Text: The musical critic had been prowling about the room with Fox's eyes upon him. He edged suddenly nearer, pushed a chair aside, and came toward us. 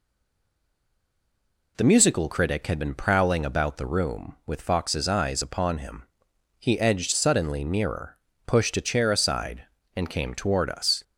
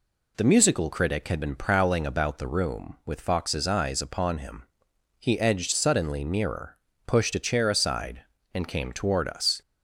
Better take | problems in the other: second | stays silent before the first word; noticeable; until 1.7 s; 1.7 s long

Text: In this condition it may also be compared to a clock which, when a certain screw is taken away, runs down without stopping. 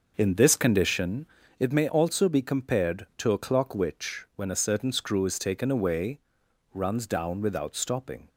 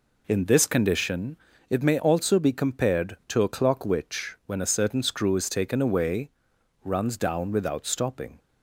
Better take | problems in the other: second | starts louder than the rest; noticeable; until 1.8 s; 6 dB // pauses between "condition" and "it"; slight; at 1.2 s; 0.32 s long; slight in the second

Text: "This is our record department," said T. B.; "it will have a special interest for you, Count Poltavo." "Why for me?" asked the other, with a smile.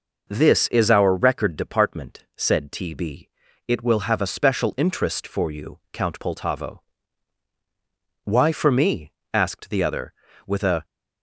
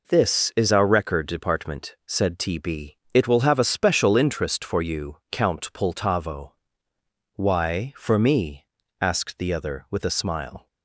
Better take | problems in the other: second | stops before "smile"; at 10.8 s

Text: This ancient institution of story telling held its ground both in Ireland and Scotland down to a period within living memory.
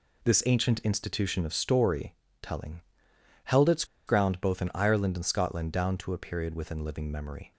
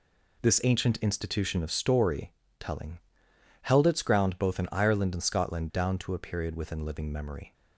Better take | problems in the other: second | pauses between "story" and "telling"; slight; at 2.1 s; 0.28 s long; slight in the second // pauses between "telling" and "held"; noticeable; at 2.8 s; 0.64 s long; noticeable in the second // pauses between "its" and "ground"; slight; at 3.8 s; 0.23 s long

